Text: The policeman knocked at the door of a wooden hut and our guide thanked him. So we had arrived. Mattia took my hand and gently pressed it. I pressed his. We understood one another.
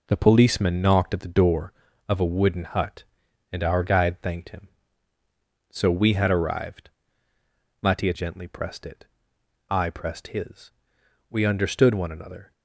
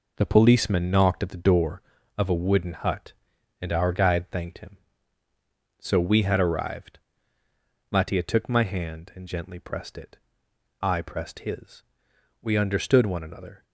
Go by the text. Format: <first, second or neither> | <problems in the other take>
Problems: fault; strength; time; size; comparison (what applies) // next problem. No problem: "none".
second | skips "took my hand and"; at 8.1 s